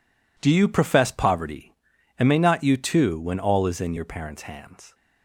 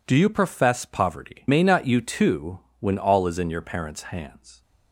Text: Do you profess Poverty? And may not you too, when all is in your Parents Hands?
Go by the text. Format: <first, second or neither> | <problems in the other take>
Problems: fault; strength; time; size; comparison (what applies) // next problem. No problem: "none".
first | skips "And"; at 1.4 s